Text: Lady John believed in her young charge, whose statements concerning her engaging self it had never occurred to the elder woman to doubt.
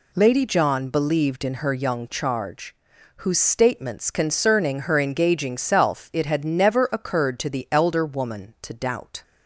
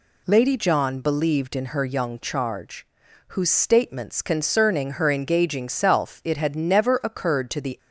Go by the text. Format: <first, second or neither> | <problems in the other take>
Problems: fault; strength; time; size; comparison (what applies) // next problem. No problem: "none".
first | stops before "elder woman to doubt"; at 7.7 s